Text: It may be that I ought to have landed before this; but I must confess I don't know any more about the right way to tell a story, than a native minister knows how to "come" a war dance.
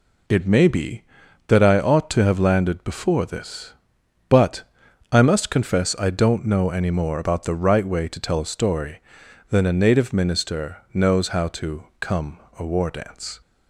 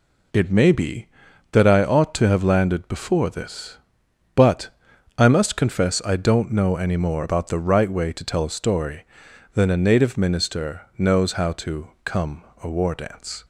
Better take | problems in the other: neither | pauses between "but" and "I"; noticeable; the same in both // pauses between "minister" and "knows"; slight; the same in both // pauses between "come" and "a"; slight; the same in both

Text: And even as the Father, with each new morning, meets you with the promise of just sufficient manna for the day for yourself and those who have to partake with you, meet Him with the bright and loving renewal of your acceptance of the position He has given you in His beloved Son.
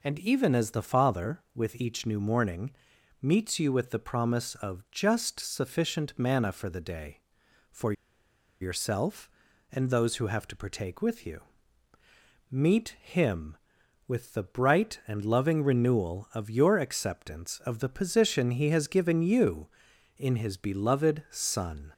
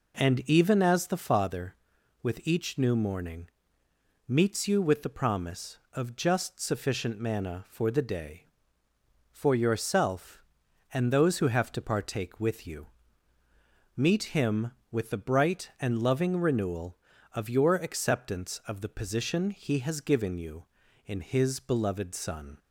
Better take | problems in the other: second | pauses between "for" and "yourself"; noticeable; at 7.9 s; 0.68 s long

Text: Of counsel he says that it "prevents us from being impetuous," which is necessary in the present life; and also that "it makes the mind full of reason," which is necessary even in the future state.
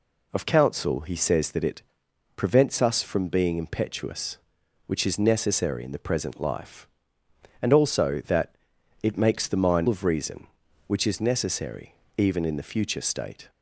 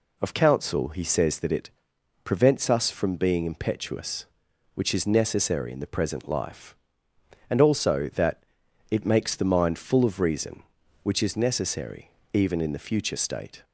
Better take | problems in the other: second | pauses between "it" and "prevents"; noticeable; at 1.8 s; 0.54 s long; noticeable in the second // pauses between "that" and "it"; noticeable; at 8.5 s; 0.48 s long; noticeable in the second // skips "full"; at 9.8 s // pauses between "necessary" and "even"; slight; at 11.9 s; 0.24 s long; slight in the second

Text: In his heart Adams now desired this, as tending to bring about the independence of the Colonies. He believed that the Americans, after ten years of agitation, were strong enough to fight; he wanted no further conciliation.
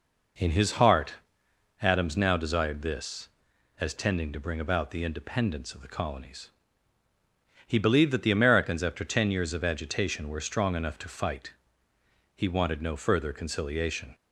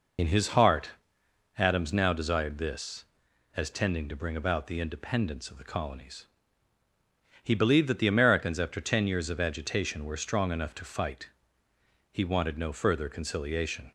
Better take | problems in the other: first | loses the start of "In"; at 0.1 s; 60 ms // pauses between "heart" and "Adams"; noticeable; at 0.9 s; 0.66 s long; noticeable in the first

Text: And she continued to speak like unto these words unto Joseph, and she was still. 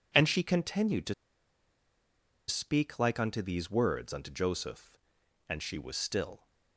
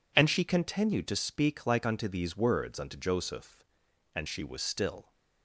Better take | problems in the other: second | pauses between "to" and "speak"; strong; at 1.1 s; 1.3 s long

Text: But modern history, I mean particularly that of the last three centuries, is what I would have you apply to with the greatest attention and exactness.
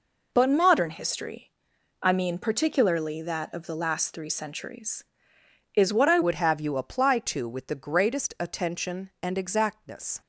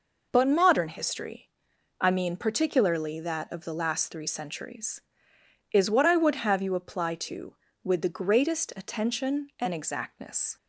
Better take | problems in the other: second | changes voice at "would"; from 6.2 s on; 4.0 s long

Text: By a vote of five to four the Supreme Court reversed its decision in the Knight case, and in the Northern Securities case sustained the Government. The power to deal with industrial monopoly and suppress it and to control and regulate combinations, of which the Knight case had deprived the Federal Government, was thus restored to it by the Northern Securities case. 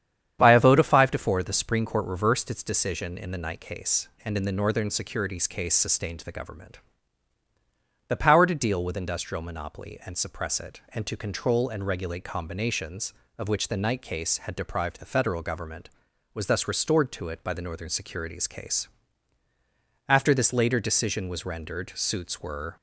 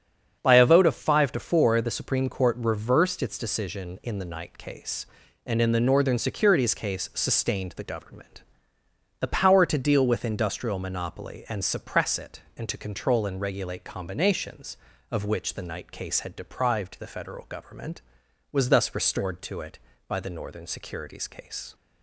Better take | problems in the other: second | starts louder than the rest; strong; until 1.4 s; 9 dB; strong in the second // goes on to say "After this later decision was rendered suits were"; strong; from 20.0 s on; 2.6 s long

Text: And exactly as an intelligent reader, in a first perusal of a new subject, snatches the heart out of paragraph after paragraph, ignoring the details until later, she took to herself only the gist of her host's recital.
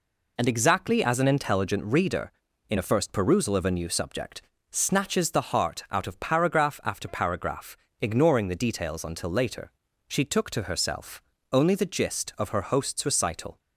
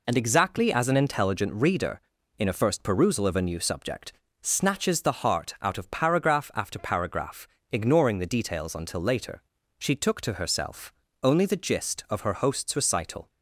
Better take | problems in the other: neither | pauses between "herself" and "only"; slight; the same in both

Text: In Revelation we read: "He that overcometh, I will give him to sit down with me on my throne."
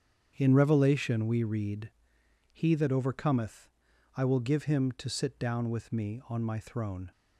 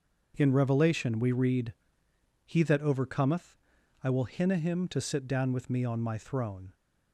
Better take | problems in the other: first | starts louder than the rest; until 1.3 s; 6.5 dB; strong in the first // says "hinna" for "give"; at 4.2 s

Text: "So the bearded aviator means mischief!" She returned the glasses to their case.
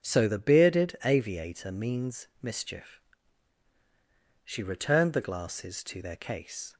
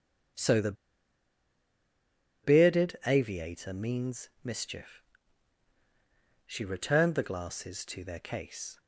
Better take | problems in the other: first | starts louder than the rest; until 3.1 s; 7 dB; also in the first // pauses between "the" and "bearded"; strong; at 0.7 s; 1.7 s long

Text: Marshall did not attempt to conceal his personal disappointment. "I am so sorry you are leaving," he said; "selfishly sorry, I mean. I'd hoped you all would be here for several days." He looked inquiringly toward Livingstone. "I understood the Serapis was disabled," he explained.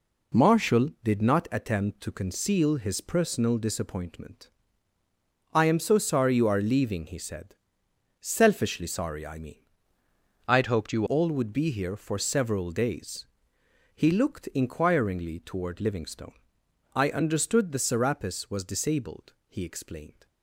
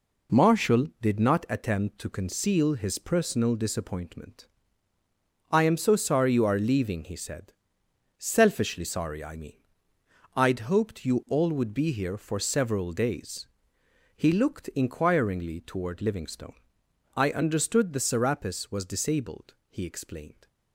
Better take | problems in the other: second | changes voice from "I'd" to "you"; from 10.4 to 11.0 s; 0.6 s long

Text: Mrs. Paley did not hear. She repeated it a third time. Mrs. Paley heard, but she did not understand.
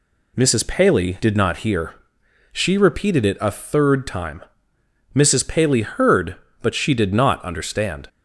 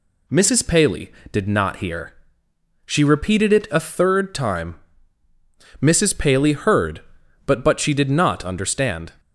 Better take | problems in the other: first | says "but" twice; at 7.6 s

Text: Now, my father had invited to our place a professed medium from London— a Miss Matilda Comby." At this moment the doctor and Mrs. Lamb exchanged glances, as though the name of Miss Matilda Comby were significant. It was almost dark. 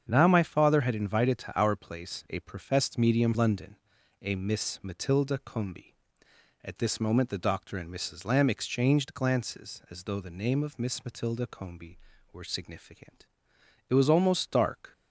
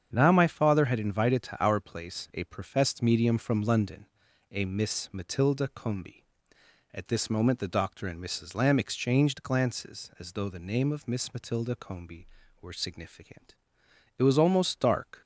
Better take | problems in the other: second | starts louder than the rest; strong; until 1.1 s; 7.5 dB; strong in the second // skips "from"; at 3.3 s

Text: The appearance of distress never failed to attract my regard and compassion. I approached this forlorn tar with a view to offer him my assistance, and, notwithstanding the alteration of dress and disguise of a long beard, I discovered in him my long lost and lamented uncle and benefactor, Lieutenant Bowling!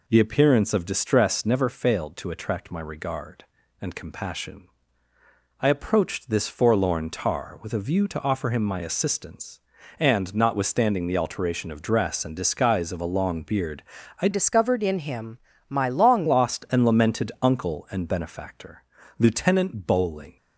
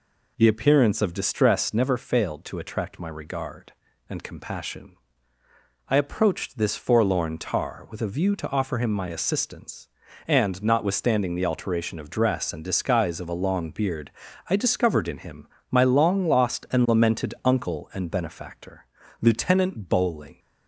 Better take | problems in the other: second | changes voice from "discovered" to "long"; from 14.3 to 16.2 s; 1.9 s long // pauses between "him" and "my"; slight; at 15.3 s; 0.32 s long; slight in the second

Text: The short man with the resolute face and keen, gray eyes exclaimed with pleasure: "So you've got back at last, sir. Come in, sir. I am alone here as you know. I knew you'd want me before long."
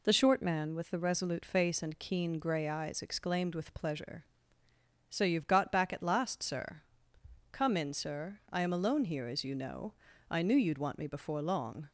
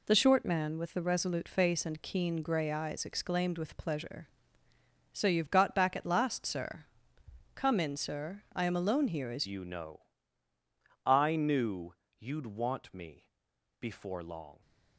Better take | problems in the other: first | changes voice at "you"; from 9.4 s on; 5.2 s long // pauses between "knew" and "you'd"; slight; at 11.9 s; 0.24 s long // pauses between "me" and "before"; noticeable; at 13.2 s; 0.52 s long

